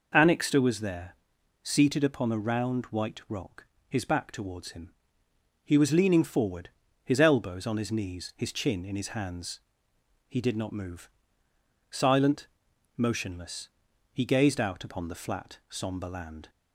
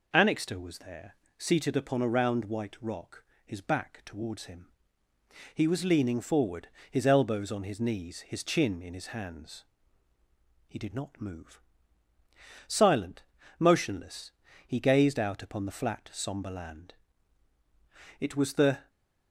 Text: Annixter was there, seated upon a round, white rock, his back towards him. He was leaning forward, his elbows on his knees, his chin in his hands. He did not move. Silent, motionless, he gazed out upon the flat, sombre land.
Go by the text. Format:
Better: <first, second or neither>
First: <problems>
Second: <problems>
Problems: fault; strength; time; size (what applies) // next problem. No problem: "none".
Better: first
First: none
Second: goes on to say "It was the"; noticeable; from 18.1 s on; 0.70 s long